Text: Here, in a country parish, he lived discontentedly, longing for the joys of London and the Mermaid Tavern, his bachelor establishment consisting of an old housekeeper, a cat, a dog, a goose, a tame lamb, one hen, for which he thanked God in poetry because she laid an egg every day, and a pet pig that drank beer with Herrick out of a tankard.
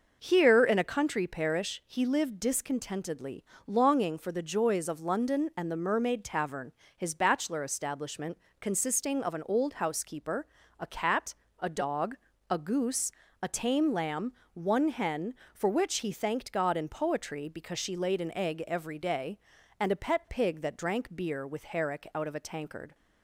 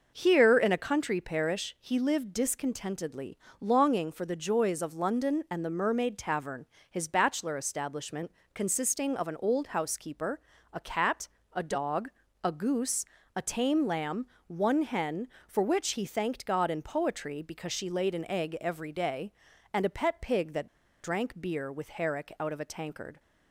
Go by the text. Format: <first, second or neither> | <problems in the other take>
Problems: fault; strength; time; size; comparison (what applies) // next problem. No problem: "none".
first | pauses between "establishment" and "consisting"; slight; at 8.2 s; 0.24 s long; slight in the first // pauses between "that" and "drank"; slight; at 20.6 s; 0.34 s long